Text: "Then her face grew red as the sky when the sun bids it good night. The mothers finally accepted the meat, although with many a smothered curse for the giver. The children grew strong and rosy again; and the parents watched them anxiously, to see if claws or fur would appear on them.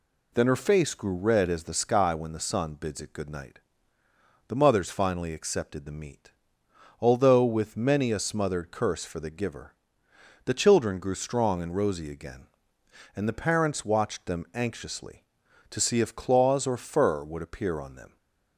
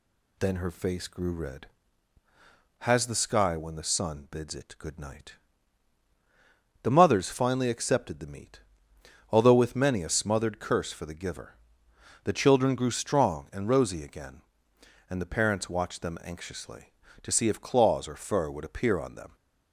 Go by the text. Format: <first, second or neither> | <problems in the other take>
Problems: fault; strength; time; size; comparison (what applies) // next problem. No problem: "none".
first | says "has" for "as"; at 2.7 s